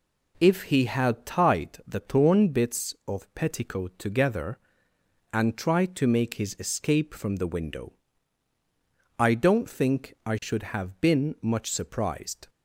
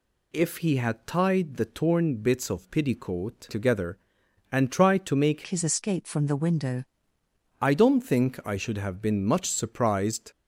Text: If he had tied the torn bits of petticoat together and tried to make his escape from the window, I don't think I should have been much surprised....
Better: first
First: none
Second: changes voice from "his" to "window"; from 5.4 to 6.8 s; 1.4 s long

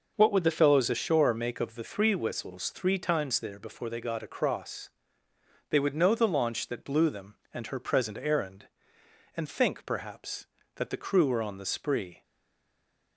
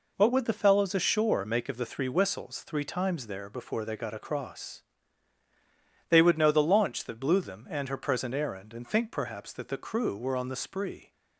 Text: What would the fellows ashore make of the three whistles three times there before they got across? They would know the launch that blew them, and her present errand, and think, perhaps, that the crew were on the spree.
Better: second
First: stays silent after the last word; from 12.2 s on; 0.9 s long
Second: none

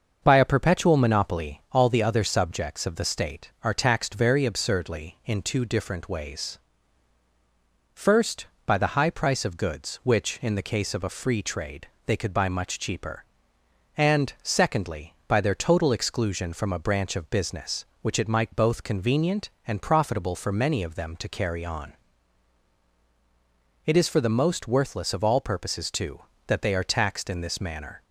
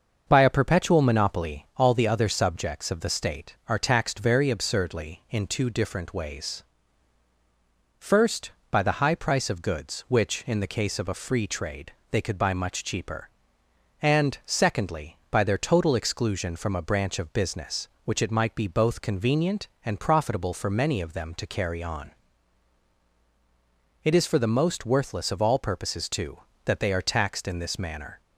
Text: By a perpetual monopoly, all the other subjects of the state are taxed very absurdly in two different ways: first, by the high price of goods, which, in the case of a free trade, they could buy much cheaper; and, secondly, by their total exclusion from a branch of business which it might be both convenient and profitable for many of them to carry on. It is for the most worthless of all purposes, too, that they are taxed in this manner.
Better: second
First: starts louder than the rest; until 1.2 s; 6.5 dB // skips "be"; at 18.5 s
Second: starts louder than the rest; until 1.2 s; 6.5 dB

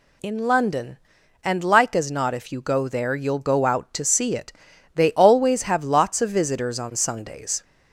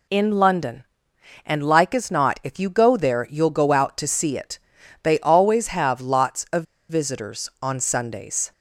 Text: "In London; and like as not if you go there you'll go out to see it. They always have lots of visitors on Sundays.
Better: first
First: none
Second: pauses between "of" and "visitors"; slight; at 6.6 s; 0.25 s long

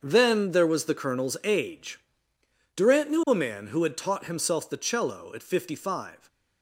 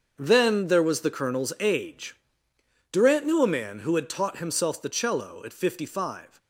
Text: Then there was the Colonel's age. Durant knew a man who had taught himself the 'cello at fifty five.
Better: neither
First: starts louder than the rest; until 1.0 s; 6.5 dB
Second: starts louder than the rest; until 1.1 s; 6.5 dB

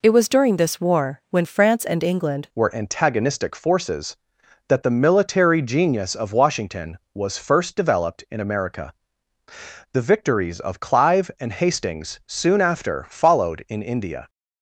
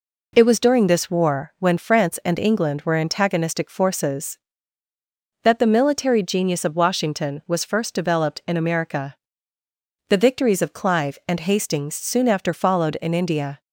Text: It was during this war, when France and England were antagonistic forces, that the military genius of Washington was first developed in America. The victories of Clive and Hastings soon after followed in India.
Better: second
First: changes voice at "were"; from 2.5 s on; 11.7 s long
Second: none

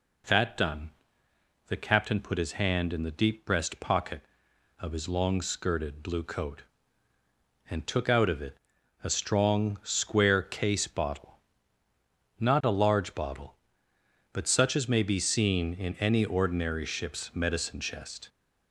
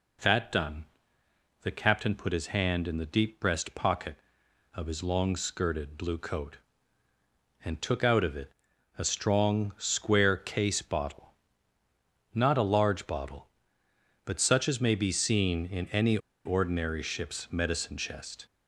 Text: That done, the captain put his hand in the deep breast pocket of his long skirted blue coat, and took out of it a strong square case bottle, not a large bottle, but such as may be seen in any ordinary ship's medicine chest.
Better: first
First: pauses between "it" and "a"; noticeable; at 8.5 s; 0.46 s long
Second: pauses between "it" and "a"; noticeable; at 8.5 s; 0.46 s long // pauses between "any" and "ordinary"; slight; at 16.1 s; 0.27 s long

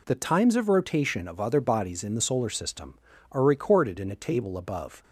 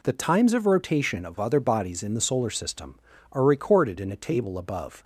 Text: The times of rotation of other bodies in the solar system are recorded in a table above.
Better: neither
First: none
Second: none

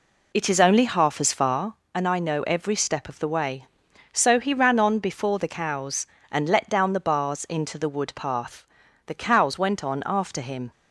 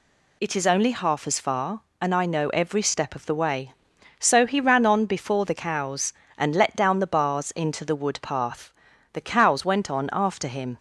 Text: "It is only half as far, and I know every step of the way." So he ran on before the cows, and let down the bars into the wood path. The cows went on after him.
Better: second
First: starts louder than the rest; slight; until 1.8 s; 3 dB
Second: none

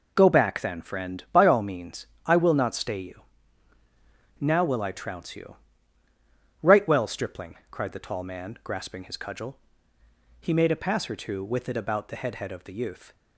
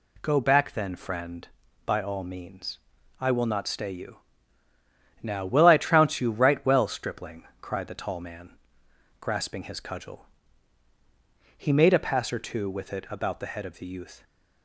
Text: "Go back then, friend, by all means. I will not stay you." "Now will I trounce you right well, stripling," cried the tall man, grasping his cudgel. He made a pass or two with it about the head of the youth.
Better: second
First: pauses between "you" and "right"; at 5.5 s; 1.0 s long // says "head" twice; at 12.3 s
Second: none

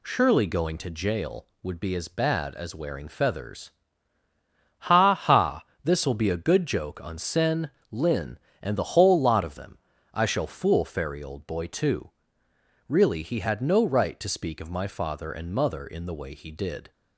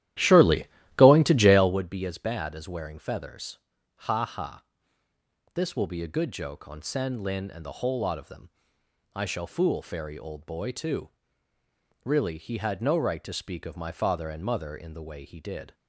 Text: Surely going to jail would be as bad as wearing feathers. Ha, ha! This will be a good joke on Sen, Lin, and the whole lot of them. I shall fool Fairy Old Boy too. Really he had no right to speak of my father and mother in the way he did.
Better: first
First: none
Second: starts louder than the rest; strong; until 1.8 s; 13.5 dB // pauses between "Surely" and "going"; slight; at 0.6 s; 0.30 s long

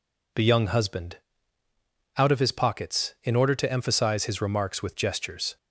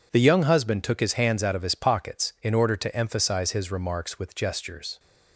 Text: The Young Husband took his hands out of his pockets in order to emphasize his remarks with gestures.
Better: second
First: skips "took his hands"; at 1.6 s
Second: none

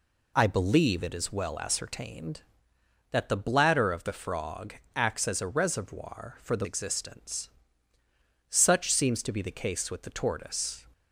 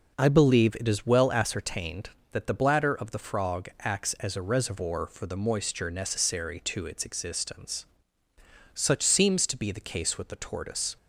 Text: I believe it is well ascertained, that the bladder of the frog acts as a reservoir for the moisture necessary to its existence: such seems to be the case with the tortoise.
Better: second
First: pauses between "frog" and "acts"; slight; at 4.7 s; 0.22 s long // skips "moisture necessary to its"; at 6.6 s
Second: none

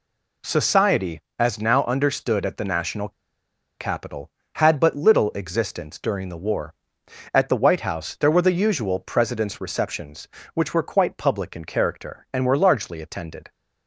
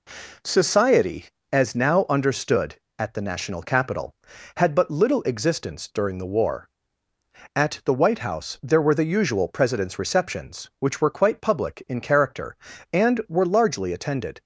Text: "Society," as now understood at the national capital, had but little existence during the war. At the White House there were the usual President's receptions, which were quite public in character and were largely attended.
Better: second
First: pauses between "national" and "capital"; noticeable; at 3.0 s; 0.69 s long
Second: none

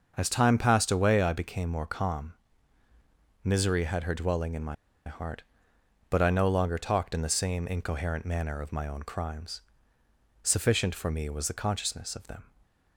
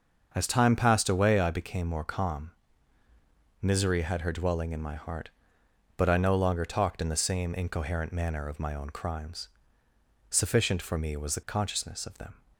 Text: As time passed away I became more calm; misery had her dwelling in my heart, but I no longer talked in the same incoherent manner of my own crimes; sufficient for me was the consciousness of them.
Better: second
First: starts louder than the rest; until 1.1 s; 6 dB // pauses between "my" and "heart"; slight; at 4.7 s; 0.32 s long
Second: starts louder than the rest; until 1.3 s; 6 dB

